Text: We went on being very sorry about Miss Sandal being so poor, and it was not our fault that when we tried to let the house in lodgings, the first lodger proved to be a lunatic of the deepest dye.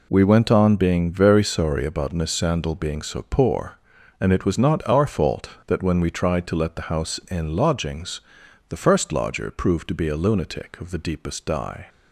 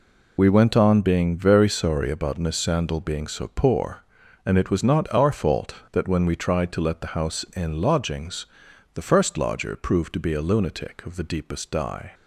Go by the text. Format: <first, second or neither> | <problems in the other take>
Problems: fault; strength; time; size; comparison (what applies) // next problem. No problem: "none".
first | loses the start of "We"; at 0.3 s; 25 ms